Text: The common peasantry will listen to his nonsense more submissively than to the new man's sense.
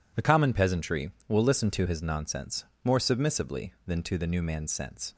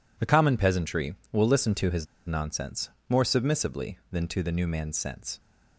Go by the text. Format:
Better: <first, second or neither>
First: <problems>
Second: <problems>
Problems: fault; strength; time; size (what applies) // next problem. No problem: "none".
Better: first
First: pauses between "nonsense" and "more"; slight; at 2.6 s; 0.20 s long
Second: pauses between "his" and "nonsense"; slight; at 2.0 s; 0.22 s long // pauses between "nonsense" and "more"; slight; at 2.8 s; 0.20 s long